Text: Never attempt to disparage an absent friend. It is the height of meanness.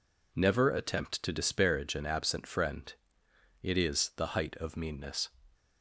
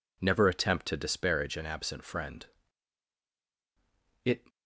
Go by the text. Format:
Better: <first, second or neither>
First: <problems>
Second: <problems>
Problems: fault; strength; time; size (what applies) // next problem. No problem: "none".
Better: first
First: none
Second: stops before "is the height of meanness"; at 4.4 s